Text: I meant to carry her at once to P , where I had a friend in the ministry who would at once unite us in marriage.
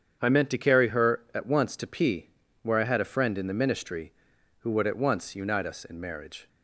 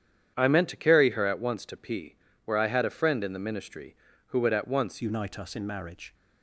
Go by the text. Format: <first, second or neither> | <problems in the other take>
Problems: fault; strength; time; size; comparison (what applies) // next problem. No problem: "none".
first | starts louder than the rest; strong; until 1.3 s; 9 dB; strong in the first // changes voice at "unite"; from 4.9 s on; 1.2 s long